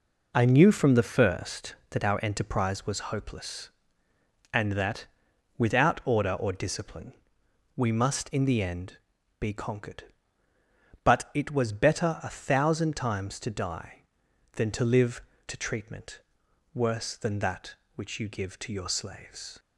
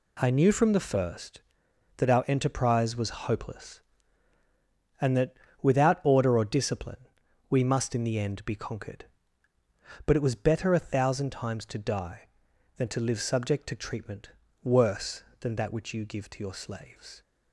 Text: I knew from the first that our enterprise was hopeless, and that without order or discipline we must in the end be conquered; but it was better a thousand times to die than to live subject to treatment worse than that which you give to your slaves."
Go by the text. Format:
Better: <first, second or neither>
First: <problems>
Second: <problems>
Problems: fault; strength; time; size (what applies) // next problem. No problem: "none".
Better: second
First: pauses between "that" and "without"; noticeable; at 5.0 s; 0.50 s long // pauses between "discipline" and "we"; noticeable; at 7.1 s; 0.64 s long // pauses between "end" and "be"; noticeable; at 8.9 s; 0.46 s long // skips "subject"; at 15.3 s // pauses between "treatment" and "worse"; noticeable; at 16.2 s; 0.54 s long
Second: pauses between "that" and "without"; slight; at 5.3 s; 0.30 s long // pauses between "discipline" and "we"; at 7.0 s; 0.44 s long // pauses between "treatment" and "worse"; slight; at 14.3 s; 0.32 s long